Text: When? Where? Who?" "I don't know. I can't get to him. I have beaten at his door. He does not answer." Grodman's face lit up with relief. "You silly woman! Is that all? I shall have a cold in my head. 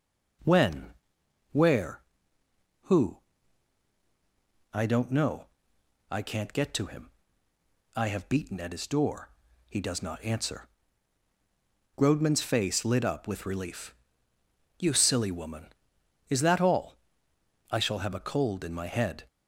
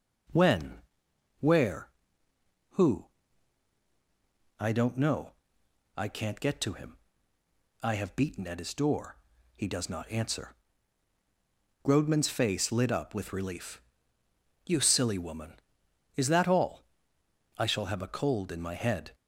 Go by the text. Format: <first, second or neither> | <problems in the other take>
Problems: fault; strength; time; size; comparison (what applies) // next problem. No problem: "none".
neither | none